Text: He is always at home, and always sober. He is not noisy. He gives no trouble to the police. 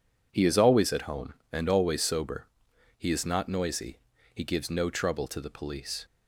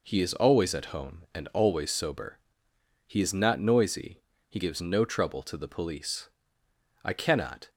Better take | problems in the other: first | goes on to say "I cannot"; noticeable; from 7.0 s on; 0.64 s long

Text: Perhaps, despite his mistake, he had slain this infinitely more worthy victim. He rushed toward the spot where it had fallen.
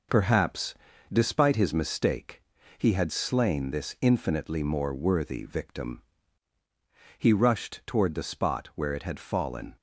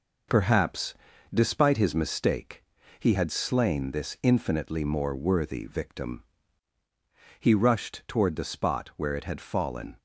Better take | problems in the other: neither | none

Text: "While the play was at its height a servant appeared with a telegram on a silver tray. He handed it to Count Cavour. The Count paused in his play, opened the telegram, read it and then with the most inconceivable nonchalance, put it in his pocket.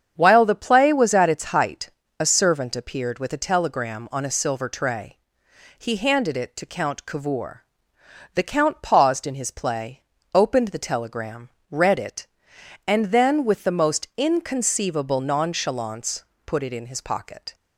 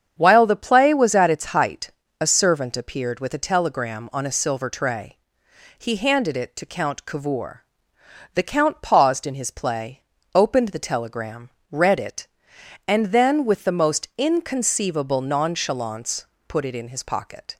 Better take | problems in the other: neither | starts louder than the rest; strong; the same in both // pauses between "height" and "a"; slight; the same in both

